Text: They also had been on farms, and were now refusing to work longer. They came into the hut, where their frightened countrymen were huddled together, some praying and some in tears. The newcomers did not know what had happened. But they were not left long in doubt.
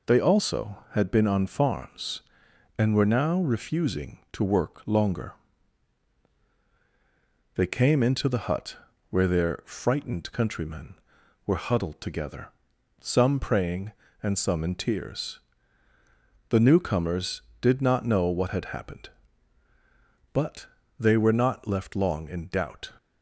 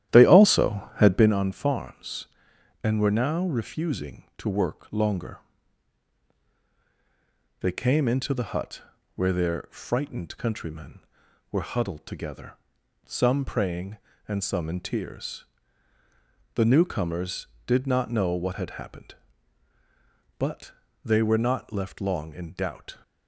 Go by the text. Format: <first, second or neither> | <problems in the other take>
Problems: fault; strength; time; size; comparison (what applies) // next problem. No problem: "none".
first | starts louder than the rest; strong; until 1.4 s; 12 dB // pauses between "But" and "they"; slight; at 20.7 s; 0.34 s long; slight in the first